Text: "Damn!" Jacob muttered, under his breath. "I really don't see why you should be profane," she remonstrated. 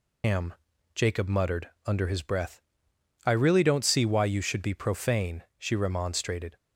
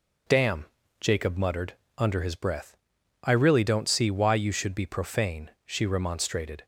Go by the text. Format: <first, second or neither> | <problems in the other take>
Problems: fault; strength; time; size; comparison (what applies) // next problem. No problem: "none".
second | loses the start of "Damn"; at 0.2 s; 160 ms